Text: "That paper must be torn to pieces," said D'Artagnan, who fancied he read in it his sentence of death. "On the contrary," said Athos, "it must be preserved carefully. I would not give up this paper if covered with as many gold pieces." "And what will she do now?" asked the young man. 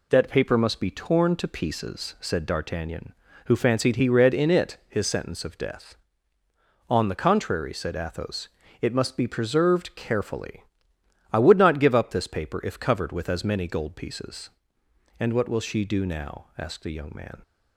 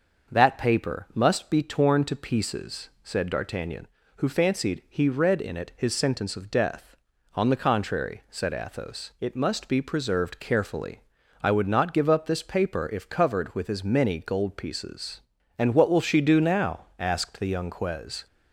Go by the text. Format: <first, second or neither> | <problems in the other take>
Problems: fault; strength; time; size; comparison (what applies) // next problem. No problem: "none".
first | starts louder than the rest; until 1.3 s; 6.5 dB // says "quez" for "man"; at 17.6 s